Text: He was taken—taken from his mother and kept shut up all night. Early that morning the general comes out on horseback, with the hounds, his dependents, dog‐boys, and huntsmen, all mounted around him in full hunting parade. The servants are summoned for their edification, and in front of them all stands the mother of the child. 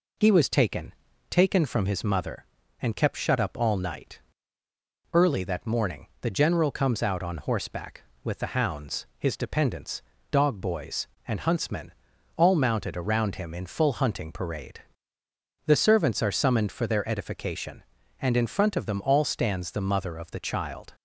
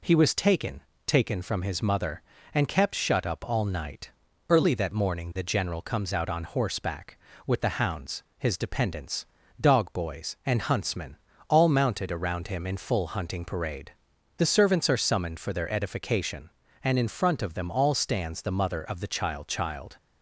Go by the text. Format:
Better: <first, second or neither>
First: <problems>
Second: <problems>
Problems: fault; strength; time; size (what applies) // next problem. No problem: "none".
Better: first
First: none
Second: says "child" twice; at 19.4 s